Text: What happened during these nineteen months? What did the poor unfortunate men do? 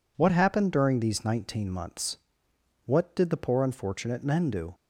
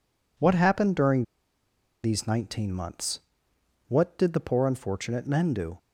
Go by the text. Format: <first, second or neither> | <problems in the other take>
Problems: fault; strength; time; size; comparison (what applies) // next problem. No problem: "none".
first | pauses between "during" and "these"; noticeable; at 1.2 s; 0.80 s long